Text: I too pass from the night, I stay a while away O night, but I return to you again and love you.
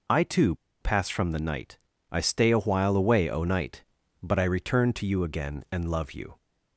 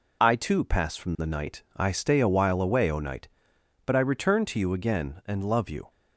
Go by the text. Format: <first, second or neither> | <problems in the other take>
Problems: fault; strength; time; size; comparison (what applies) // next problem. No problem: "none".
second | pauses between "too" and "pass"; slight; at 0.5 s; 0.25 s long